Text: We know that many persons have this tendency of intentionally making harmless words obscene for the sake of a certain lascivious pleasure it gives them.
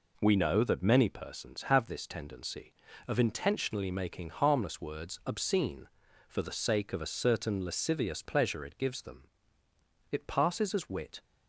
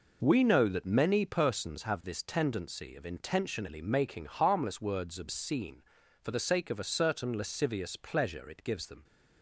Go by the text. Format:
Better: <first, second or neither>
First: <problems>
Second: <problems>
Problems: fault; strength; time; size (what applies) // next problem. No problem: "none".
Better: second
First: goes on to say "It passes as wit"; noticeable; from 10.1 s on; 1.1 s long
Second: none